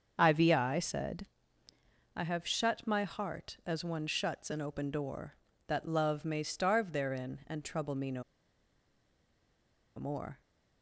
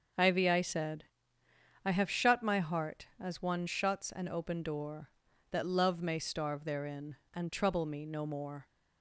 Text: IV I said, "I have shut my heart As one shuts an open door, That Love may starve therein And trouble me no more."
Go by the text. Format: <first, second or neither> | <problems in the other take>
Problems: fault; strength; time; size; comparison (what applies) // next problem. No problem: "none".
second | starts louder than the rest; until 1.1 s; 6.5 dB; also in the second // pauses between "no" and "more"; strong; at 8.2 s; 1.7 s long